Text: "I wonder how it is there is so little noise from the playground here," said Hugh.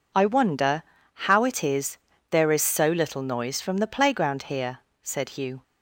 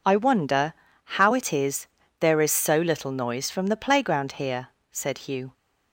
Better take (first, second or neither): neither